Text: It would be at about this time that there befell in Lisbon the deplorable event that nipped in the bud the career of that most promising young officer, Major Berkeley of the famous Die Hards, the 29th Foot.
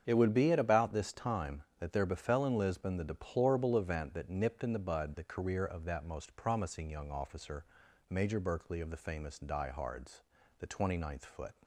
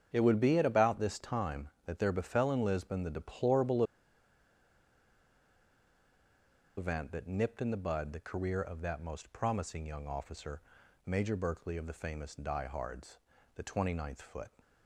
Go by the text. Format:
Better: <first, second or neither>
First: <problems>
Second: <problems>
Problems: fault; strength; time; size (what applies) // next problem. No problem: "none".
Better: first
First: starts louder than the rest; strong; until 1.0 s; 7.5 dB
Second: starts louder than the rest; strong; until 1.1 s; 7.5 dB // pauses between "deplorable" and "event"; strong; at 3.8 s; 2.9 s long